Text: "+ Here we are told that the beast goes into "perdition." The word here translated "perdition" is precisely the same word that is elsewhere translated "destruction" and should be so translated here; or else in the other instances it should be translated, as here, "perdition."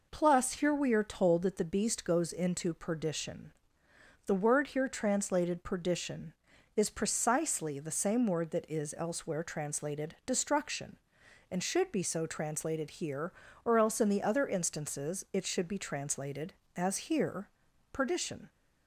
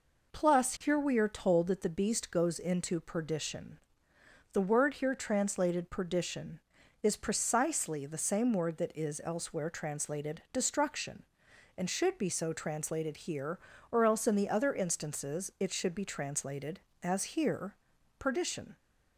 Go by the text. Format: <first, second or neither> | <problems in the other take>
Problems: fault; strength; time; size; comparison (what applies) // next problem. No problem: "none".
neither | none